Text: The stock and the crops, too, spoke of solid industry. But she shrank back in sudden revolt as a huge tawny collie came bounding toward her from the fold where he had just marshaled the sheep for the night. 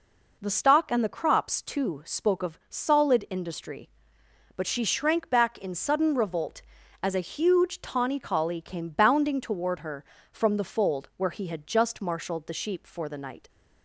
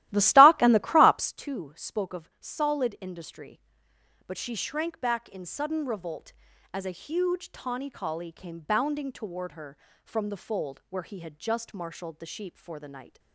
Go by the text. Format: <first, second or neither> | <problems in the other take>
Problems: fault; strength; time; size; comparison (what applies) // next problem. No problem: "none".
first | starts louder than the rest; strong; until 1.3 s; 15 dB